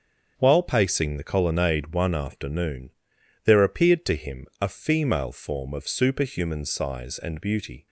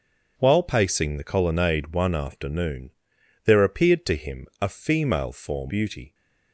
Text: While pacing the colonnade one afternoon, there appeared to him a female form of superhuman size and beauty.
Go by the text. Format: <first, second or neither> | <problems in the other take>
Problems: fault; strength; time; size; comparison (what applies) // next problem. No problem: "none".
first | starts louder than the rest; until 1.3 s; 7 dB; strong in the first // skips "of superhuman size and"; at 5.7 s